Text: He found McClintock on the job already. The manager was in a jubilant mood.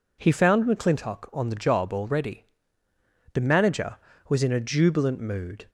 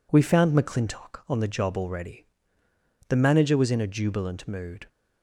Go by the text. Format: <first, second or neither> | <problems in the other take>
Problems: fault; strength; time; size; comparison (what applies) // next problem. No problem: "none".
first | says "We" for "He"; at 0.1 s